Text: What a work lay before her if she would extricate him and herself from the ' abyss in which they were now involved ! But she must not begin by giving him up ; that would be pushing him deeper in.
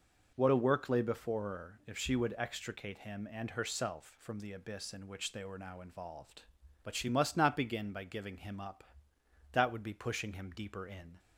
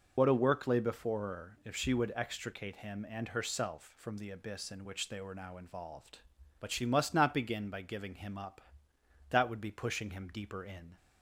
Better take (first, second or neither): first